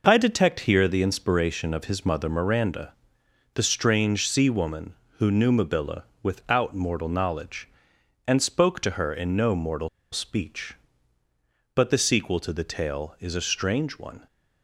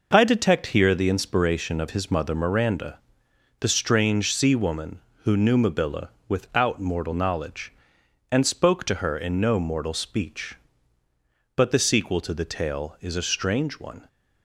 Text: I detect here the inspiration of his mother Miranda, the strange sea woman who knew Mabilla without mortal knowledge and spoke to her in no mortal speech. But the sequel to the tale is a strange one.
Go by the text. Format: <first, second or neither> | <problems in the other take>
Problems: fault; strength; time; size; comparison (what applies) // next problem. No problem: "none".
second | pauses between "Mabilla" and "without"; slight; at 6.0 s; 0.18 s long; slight in the second // pauses between "mortal" and "speech"; slight; at 9.8 s; 0.23 s long